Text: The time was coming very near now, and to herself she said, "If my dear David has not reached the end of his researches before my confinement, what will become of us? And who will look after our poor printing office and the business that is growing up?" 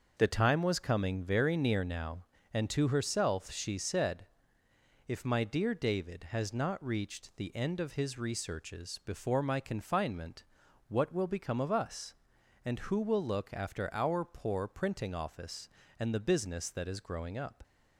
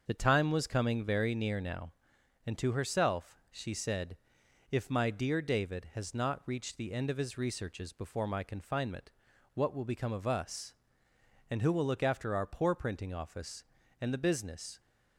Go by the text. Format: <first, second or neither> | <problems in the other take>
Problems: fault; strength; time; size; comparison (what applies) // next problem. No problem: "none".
first | starts louder than the rest; until 1.0 s; 6.5 dB; also in the first // stops before "that is growing up"; at 14.7 s